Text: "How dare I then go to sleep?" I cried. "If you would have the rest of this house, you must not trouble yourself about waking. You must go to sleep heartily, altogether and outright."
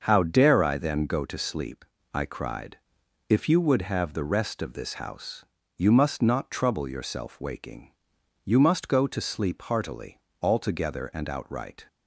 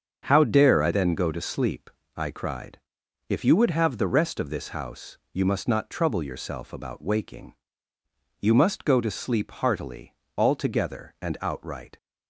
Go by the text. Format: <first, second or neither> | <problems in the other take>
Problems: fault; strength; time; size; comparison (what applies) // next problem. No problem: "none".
second | starts louder than the rest; until 1.0 s; 6 dB; also in the second // skips "about"; at 7.3 s